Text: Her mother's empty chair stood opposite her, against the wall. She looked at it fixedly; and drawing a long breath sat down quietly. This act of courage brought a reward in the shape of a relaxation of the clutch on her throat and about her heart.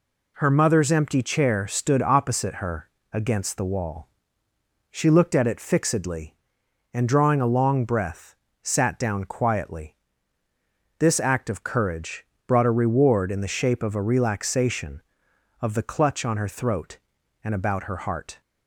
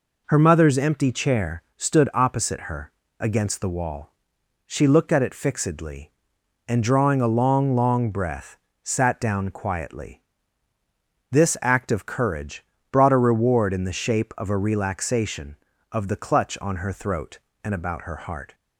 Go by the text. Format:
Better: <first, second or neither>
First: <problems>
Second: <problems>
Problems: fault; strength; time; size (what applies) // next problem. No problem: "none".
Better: first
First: pauses between "breath" and "sat"; slight; at 8.3 s; 0.26 s long // pauses between "courage" and "brought"; slight; at 12.2 s; 0.22 s long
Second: says "long" twice; at 7.7 s // pauses between "breath" and "sat"; slight; at 8.5 s; 0.26 s long // pauses between "courage" and "brought"; slight; at 12.6 s; 0.26 s long